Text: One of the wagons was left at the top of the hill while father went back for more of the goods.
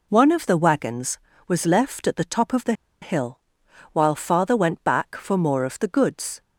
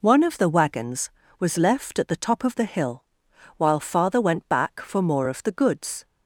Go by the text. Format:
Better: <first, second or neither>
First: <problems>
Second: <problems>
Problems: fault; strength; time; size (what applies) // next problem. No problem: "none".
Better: second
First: pauses between "the" and "hill"; slight; at 2.7 s; 0.29 s long // pauses between "hill" and "while"; noticeable; at 3.3 s; 0.54 s long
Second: pauses between "hill" and "while"; noticeable; at 3.0 s; 0.54 s long